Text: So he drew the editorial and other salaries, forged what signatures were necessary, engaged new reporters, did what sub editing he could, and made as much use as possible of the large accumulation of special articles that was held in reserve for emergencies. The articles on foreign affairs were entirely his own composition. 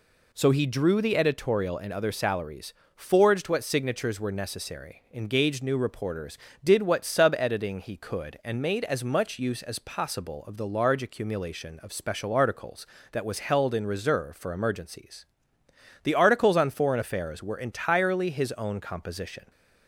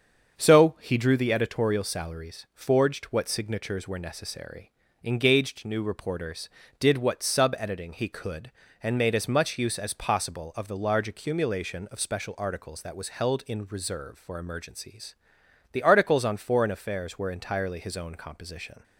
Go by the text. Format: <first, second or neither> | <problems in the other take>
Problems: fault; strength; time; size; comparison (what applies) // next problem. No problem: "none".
first | starts louder than the rest; until 1.4 s; 7 dB // skips "and other"; at 1.8 s